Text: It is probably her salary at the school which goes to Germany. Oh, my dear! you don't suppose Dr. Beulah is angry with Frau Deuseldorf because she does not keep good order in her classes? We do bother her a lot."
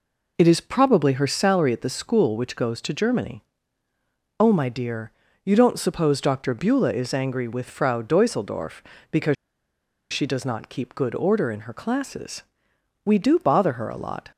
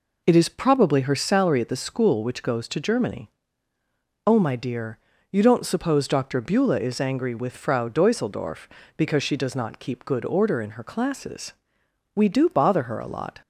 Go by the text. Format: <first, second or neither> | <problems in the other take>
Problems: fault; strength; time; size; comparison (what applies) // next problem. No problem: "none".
second | pauses between "because" and "she"; noticeable; at 9.3 s; 0.77 s long